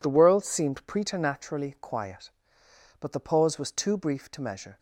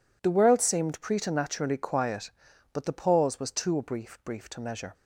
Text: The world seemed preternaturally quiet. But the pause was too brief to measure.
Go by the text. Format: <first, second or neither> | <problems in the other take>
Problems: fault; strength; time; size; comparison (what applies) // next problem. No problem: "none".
first | says "brief" twice; at 4.2 s